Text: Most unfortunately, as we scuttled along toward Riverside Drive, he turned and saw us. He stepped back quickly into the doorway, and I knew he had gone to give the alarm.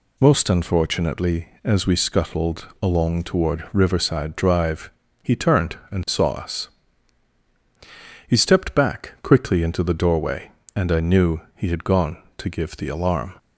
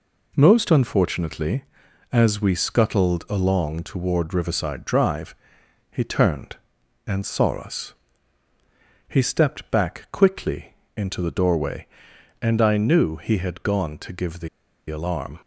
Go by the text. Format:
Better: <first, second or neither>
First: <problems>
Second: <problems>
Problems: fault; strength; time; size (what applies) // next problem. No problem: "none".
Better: first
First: none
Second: pauses between "quickly" and "into"; slight; at 10.7 s; 0.22 s long // pauses between "the" and "alarm"; at 14.4 s; 0.40 s long